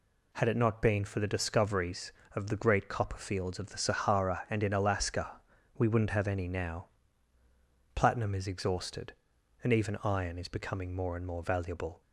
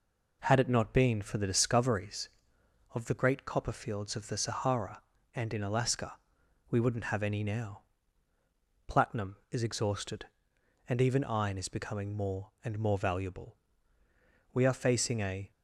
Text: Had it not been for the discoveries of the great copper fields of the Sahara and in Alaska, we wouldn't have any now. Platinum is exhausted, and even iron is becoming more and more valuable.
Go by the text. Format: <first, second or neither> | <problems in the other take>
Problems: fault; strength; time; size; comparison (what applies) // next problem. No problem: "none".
first | goes on to say "We are facing a"; noticeable; from 14.5 s on; 0.98 s long